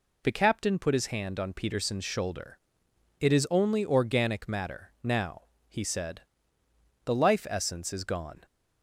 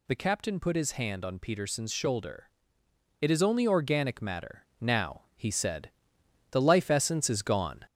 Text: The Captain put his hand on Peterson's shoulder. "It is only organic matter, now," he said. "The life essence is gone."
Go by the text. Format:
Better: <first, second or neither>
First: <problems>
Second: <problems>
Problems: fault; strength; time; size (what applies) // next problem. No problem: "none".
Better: first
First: none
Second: gets louder; slight; throughout; 3 dB